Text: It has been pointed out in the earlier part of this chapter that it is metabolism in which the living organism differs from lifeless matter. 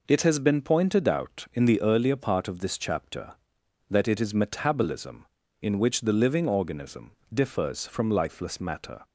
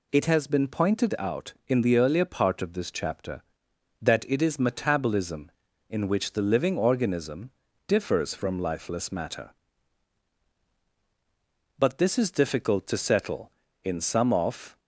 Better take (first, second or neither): first